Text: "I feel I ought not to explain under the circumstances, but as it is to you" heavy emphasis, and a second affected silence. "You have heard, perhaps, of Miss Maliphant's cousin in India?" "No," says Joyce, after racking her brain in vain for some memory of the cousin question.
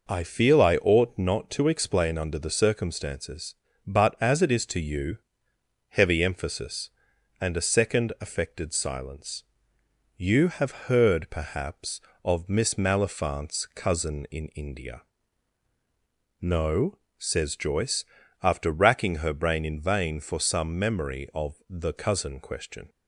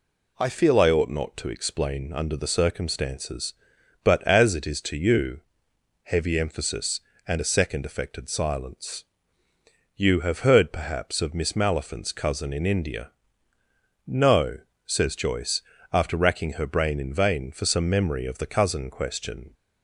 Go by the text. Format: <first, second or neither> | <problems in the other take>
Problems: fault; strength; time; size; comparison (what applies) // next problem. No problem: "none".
neither | pauses between "you" and "heavy"; noticeable; the same in both